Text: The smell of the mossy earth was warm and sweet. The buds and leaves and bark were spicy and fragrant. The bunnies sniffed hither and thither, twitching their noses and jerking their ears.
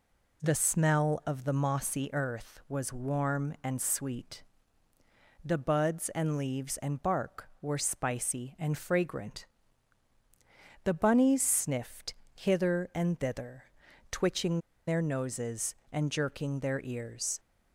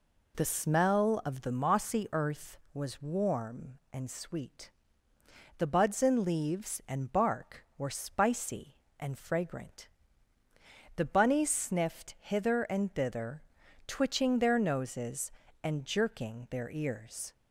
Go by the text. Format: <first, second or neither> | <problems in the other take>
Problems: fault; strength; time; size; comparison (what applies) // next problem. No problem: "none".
second | pauses between "sniffed" and "hither"; slight; at 12.1 s; 0.18 s long // pauses between "twitching" and "their"; slight; at 14.6 s; 0.26 s long